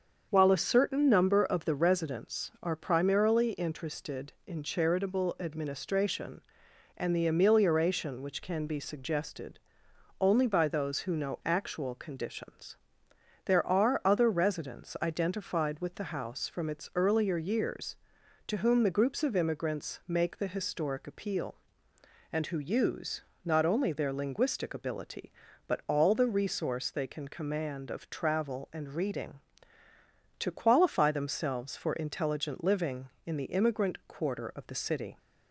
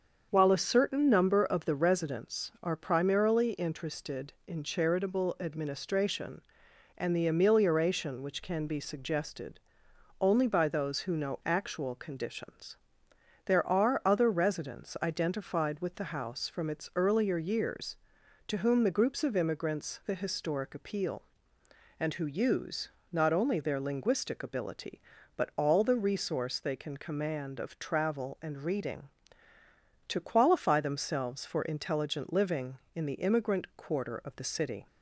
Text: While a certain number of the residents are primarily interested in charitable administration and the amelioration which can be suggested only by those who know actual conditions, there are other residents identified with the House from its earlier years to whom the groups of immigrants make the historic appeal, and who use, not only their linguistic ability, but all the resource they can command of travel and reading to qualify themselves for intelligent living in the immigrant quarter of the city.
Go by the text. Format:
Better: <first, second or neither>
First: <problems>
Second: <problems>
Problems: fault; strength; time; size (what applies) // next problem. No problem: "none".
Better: first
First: starts louder than the rest; until 1.3 s; 7 dB // pauses between "suggested" and "only"; noticeable; at 9.5 s; 0.62 s long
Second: starts louder than the rest; until 1.3 s; 7 dB // pauses between "suggested" and "only"; noticeable; at 9.5 s; 0.62 s long // skips "make"; at 20.0 s